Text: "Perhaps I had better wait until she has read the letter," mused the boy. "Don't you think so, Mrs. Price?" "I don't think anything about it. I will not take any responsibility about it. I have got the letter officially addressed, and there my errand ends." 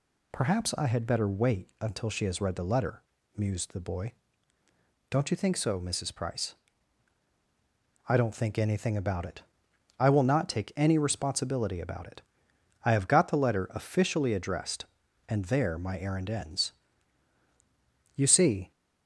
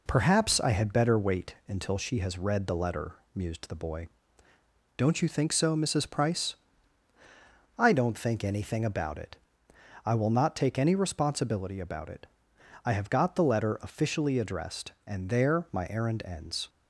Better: second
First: goes on to say "You see"; from 18.1 s on; 0.54 s long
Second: none

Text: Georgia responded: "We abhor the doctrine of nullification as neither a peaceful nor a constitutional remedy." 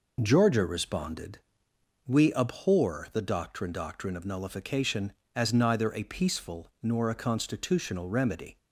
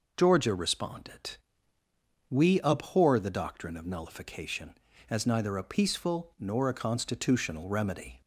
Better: second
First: says "doctrine" twice; at 3.7 s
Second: none

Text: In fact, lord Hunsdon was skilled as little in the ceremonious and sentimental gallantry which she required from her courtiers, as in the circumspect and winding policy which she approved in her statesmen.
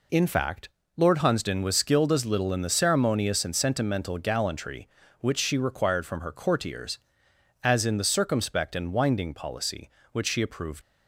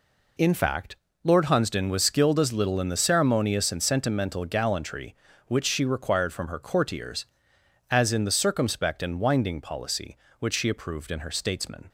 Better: second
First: stops before "in her statesmen"; at 10.8 s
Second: none

